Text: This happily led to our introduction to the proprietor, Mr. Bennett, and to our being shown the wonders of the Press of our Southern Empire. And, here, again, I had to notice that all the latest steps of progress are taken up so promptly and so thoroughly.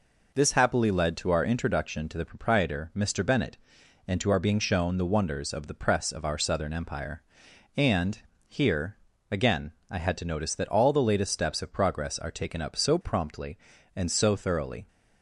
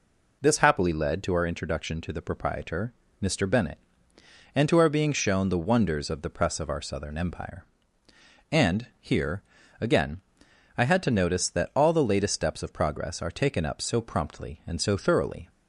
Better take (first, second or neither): neither